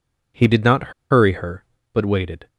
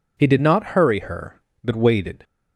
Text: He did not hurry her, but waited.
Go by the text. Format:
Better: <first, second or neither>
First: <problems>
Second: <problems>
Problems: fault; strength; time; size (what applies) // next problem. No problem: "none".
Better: second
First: pauses between "not" and "hurry"; slight; at 0.9 s; 0.19 s long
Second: none